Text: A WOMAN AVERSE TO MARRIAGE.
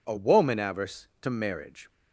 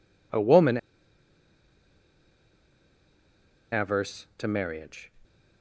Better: first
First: none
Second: pauses between "WOMAN" and "AVERSE"; strong; at 0.7 s; 2.9 s long

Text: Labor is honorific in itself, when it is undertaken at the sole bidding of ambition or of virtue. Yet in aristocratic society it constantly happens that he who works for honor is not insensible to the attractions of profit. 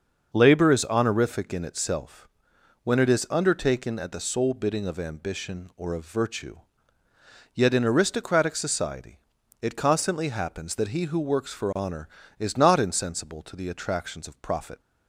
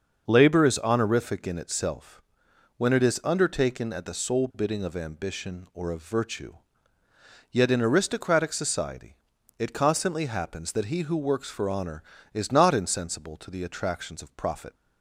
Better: neither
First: starts louder than the rest; until 1.3 s; 6 dB // pauses between "society" and "it"; at 9.1 s; 0.42 s long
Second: starts louder than the rest; until 1.3 s; 6 dB // pauses between "society" and "it"; at 9.1 s; 0.42 s long

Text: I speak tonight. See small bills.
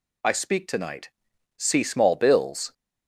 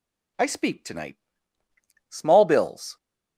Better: first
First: none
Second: skips "See"; at 1.6 s

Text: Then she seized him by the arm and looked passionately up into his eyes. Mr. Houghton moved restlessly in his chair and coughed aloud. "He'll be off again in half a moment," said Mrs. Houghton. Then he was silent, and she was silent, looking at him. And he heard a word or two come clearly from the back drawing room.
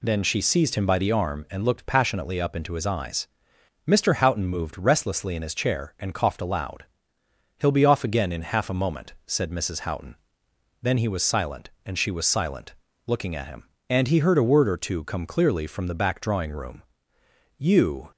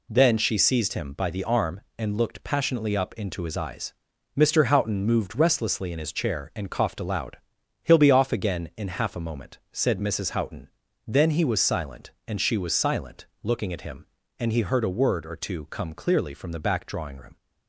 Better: second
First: goes on to say "You"; from 17.5 s on; 0.54 s long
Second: none

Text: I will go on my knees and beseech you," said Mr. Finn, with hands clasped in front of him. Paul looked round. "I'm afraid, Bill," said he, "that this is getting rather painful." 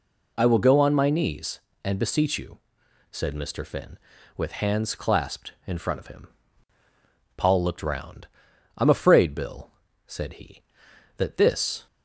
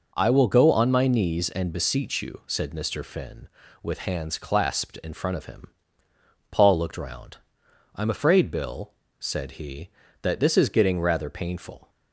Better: second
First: stops before "is getting rather painful"; at 11.8 s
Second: none

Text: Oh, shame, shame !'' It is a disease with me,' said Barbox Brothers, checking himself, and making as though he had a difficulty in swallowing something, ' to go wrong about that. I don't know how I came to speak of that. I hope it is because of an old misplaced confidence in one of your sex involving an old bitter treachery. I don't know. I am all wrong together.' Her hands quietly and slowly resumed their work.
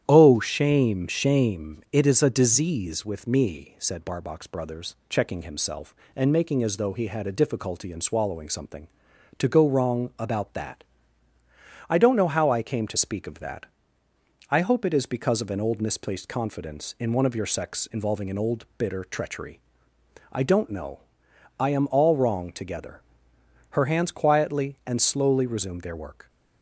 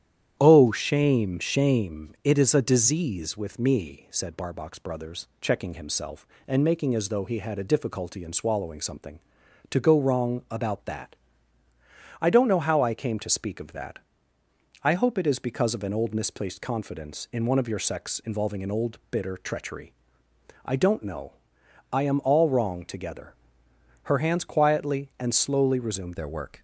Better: first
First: starts louder than the rest; strong; until 1.0 s; 10 dB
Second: starts louder than the rest; strong; until 1.4 s; 10 dB // changes voice at "their"; from 26.1 s on; 0.5 s long

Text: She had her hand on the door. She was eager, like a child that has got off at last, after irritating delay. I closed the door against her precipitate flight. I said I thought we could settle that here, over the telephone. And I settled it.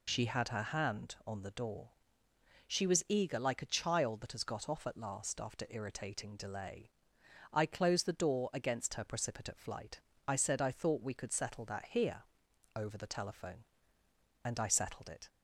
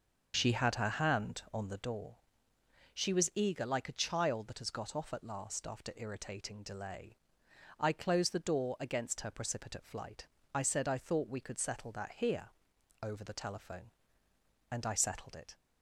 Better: first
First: none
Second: starts louder than the rest; noticeable; until 2.0 s; 6 dB

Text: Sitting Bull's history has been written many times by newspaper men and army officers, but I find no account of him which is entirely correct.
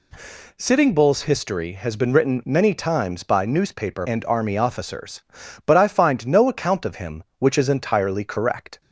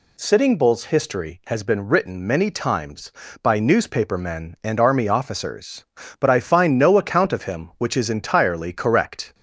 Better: second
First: skips "men"; at 4.0 s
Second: none

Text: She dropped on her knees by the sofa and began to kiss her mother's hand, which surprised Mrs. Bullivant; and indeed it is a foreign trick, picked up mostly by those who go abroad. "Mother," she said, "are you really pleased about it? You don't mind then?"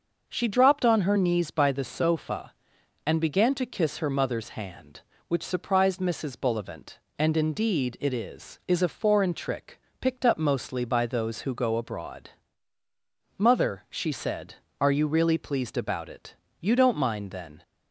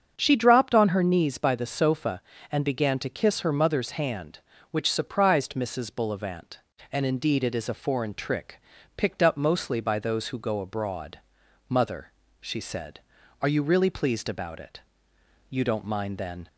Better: second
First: starts louder than the rest; until 1.2 s; 6 dB // says "is" twice; at 8.6 s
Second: starts louder than the rest; strong; until 1.1 s; 7.5 dB

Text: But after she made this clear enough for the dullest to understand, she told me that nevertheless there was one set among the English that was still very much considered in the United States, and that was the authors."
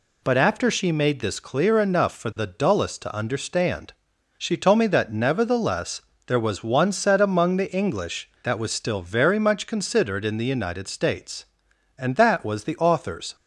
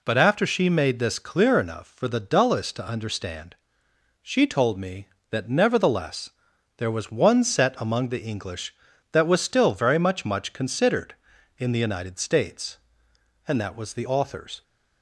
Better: first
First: pauses between "nevertheless" and "there"; slight; at 6.0 s; 0.26 s long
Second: pauses between "nevertheless" and "there"; noticeable; at 6.2 s; 0.48 s long // says "much" twice; at 10.2 s

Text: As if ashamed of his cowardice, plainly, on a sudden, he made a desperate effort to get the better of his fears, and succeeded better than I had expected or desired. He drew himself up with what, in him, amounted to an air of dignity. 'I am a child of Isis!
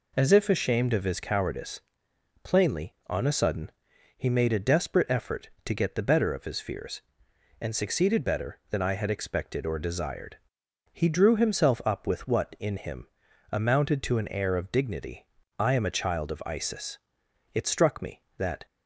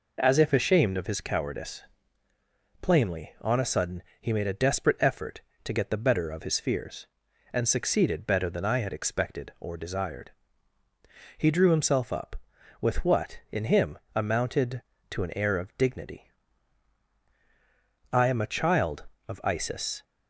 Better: second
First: goes on to say "It struck me that"; noticeable; from 17.5 s on; 1.1 s long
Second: none

